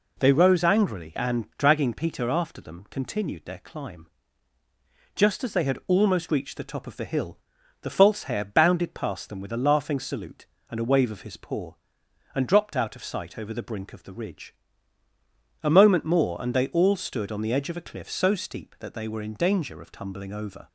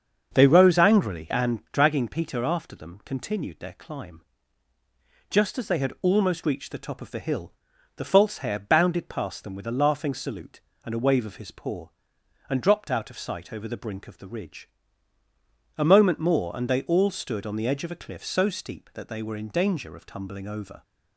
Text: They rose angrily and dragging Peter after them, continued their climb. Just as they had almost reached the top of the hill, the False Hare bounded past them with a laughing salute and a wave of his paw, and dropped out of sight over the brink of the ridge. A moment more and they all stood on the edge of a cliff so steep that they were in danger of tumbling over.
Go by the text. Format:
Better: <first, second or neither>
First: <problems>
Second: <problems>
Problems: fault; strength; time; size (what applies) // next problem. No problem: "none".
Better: first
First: none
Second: starts louder than the rest; until 1.6 s; 6.5 dB